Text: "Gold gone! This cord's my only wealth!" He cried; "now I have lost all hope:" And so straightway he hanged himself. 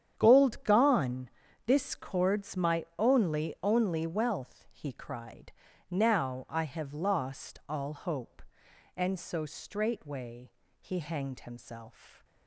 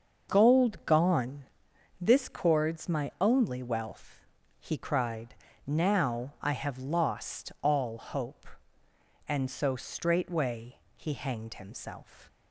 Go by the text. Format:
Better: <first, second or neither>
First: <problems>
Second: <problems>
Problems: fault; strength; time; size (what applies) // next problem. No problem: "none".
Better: second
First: starts louder than the rest; strong; until 1.1 s; 9 dB // says "only" twice; at 3.6 s // pauses between "straightway" and "he"; slight; at 10.5 s; 0.28 s long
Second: starts louder than the rest; until 1.3 s; 6 dB // pauses between "straightway" and "he"; slight; at 10.7 s; 0.18 s long